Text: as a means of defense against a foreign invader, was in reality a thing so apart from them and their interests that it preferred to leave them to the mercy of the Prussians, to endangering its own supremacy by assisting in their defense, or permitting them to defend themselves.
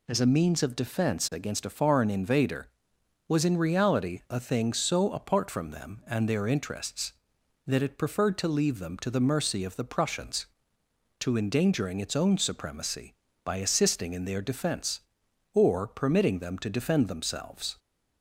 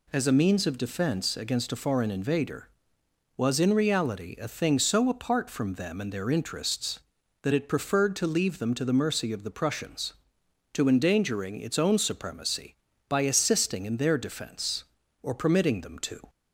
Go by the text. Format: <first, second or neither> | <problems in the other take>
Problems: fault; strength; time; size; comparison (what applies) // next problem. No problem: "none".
first | stops before "defend themselves"; at 16.2 s